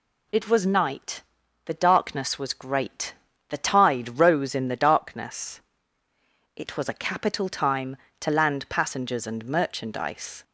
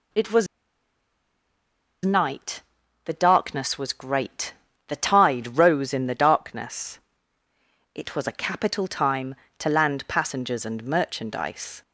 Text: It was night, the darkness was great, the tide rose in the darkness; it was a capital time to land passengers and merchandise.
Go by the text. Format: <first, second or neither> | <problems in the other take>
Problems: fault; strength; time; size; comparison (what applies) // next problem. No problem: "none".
first | pauses between "was" and "night"; strong; at 0.4 s; 1.5 s long